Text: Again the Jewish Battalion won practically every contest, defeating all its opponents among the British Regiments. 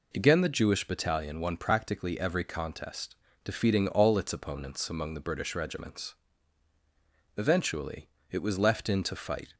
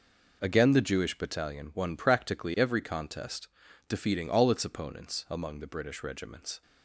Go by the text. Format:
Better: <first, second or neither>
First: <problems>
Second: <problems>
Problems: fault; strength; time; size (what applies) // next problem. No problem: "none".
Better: second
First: goes on to say "Eventually it was left in to fight"; strong; from 7.3 s on; 2.1 s long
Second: none